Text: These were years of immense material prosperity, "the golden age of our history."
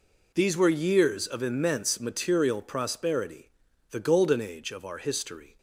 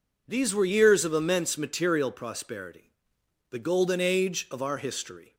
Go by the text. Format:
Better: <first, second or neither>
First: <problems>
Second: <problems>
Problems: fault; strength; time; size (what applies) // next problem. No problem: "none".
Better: neither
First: none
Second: none